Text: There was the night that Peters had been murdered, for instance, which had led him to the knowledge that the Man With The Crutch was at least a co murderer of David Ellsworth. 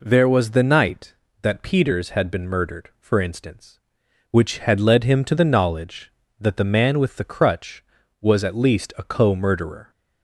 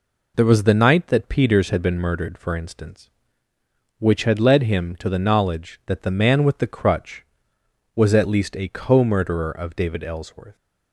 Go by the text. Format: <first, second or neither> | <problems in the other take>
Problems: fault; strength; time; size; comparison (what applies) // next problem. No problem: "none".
second | stops before "of David Ellsworth"; at 9.9 s